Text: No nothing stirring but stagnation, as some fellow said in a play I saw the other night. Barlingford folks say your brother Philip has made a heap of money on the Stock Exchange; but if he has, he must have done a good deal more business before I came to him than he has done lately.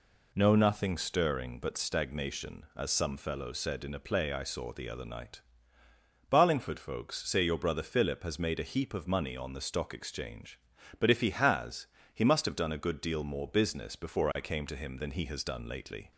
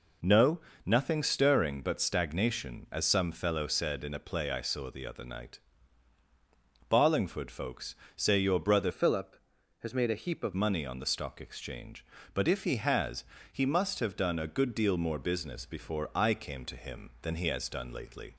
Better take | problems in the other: first | pauses between "No" and "nothing"; slight; at 0.5 s; 0.26 s long // pauses between "folks" and "say"; slight; at 7.9 s; 0.22 s long // changes voice from "Philip" to "of"; from 8.9 to 10.5 s; 1.6 s long

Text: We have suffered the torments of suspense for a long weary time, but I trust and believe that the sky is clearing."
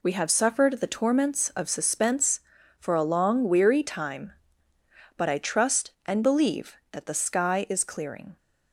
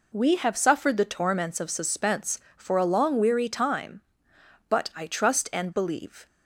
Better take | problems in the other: first | stops before "that the sky is clearing"; at 6.2 s

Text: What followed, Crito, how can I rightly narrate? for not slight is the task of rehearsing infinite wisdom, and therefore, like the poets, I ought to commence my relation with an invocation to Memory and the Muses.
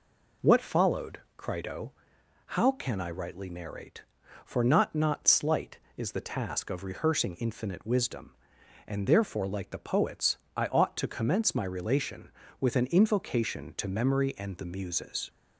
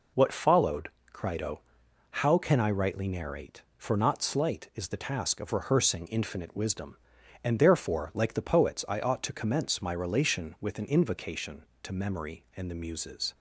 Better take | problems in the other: second | says "not" twice; at 4.9 s

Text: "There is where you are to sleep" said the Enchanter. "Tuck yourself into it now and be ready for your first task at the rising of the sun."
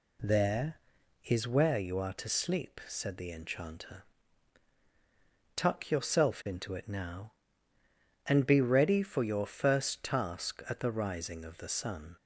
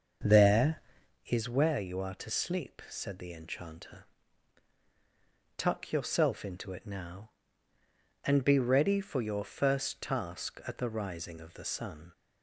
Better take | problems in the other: first | starts louder than the rest; until 1.1 s; 6.5 dB

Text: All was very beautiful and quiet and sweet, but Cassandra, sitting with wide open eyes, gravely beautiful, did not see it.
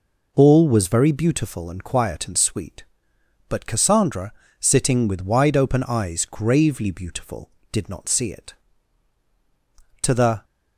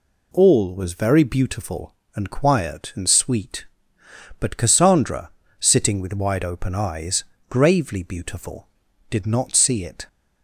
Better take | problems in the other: second | goes on to say "To the"; slight; from 10.0 s on; 0.42 s long

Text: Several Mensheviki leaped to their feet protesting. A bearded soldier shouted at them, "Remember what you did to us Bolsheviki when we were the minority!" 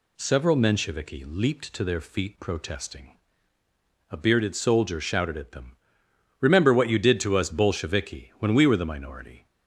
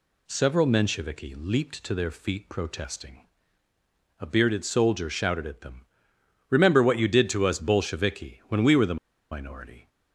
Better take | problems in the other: first | pauses between "the" and "minority"; slight; at 8.9 s; 0.35 s long

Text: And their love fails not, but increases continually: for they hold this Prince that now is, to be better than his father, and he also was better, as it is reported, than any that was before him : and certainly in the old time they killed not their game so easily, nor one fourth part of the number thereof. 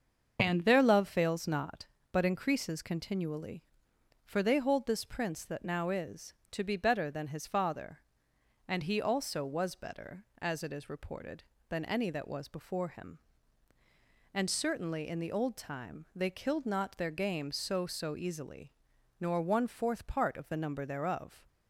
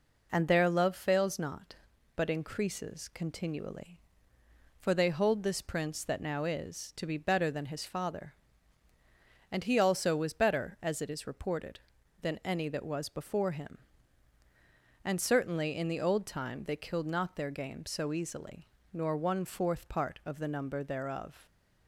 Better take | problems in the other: second | starts louder than the rest; until 1.4 s; 7 dB // says "so" twice; at 17.8 s

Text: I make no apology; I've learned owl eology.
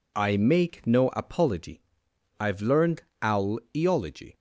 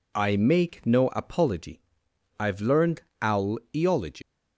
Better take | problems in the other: first | pauses between "learned" and "owl"; slight; at 3.0 s; 0.20 s long; slight in the first // pauses between "owl" and "eology"; slight; at 3.5 s; 0.16 s long; slight in the first // leaves "eology" unfinished; at 4.2 s; 110 ms

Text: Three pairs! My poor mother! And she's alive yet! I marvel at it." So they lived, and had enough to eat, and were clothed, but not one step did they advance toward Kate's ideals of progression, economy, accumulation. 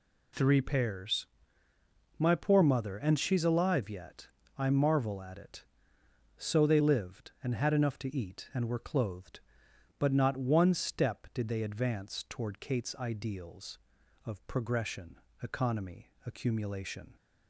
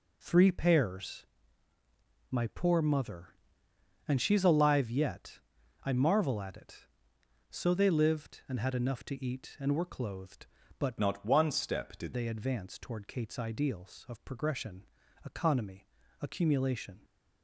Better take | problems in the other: first | changes voice from "not" to "did"; from 10.9 to 12.1 s; 1.2 s long

